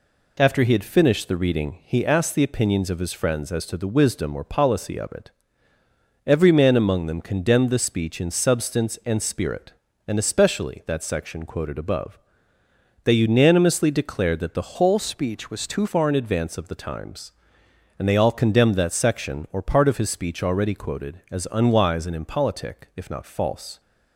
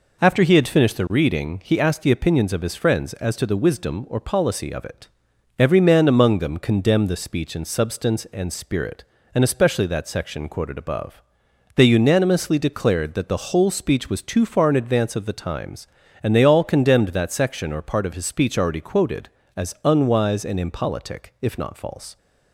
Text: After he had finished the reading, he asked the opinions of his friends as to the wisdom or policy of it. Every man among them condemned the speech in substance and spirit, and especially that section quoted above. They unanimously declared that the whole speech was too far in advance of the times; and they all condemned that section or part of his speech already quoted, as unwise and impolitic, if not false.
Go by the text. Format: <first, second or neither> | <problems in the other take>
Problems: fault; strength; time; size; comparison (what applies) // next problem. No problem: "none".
second | changes voice from "whole" to "too"; from 14.7 to 15.8 s; 1.1 s long